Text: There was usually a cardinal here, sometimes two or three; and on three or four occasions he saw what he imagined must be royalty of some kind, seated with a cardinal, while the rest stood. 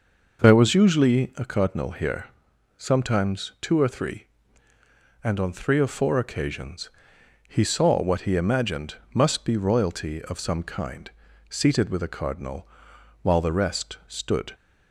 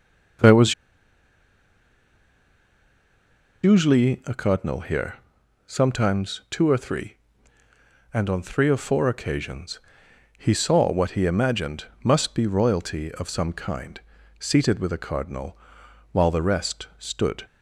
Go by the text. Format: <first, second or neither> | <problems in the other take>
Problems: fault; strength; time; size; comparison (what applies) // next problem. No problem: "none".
first | pauses between "was" and "usually"; strong; at 0.7 s; 2.8 s long // pauses between "occasions" and "he"; noticeable; at 9.7 s; 0.58 s long; noticeable in the first // pauses between "imagined" and "must"; slight; at 11.8 s; 0.18 s long; slight in the first